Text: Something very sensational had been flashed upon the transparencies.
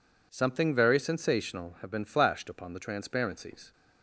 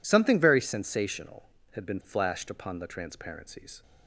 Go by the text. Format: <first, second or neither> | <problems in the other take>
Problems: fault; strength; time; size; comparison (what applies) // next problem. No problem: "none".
second | says "have" for "had"; at 1.8 s